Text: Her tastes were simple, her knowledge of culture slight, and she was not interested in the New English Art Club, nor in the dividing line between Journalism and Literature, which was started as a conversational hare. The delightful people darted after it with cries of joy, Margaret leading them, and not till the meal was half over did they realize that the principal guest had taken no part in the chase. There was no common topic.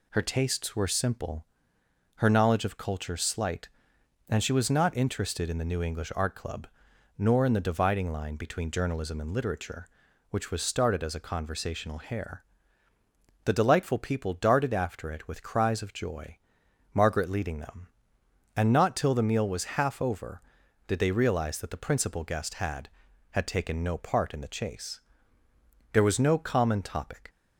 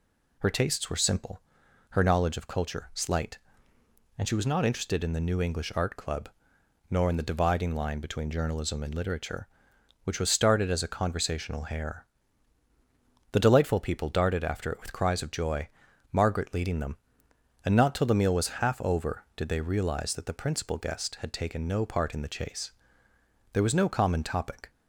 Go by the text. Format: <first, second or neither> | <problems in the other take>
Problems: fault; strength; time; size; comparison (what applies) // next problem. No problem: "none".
second | says "had" twice; at 23.3 s